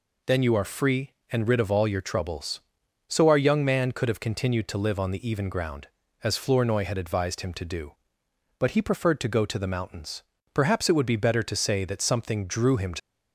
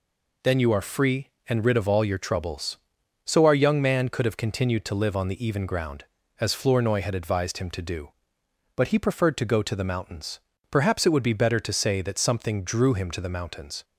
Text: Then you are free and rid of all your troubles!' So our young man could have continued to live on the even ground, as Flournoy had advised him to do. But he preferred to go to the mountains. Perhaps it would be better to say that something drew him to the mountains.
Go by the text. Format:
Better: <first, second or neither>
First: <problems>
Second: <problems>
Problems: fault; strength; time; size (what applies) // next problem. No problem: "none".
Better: second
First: stops before "the mountains"; at 12.9 s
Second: none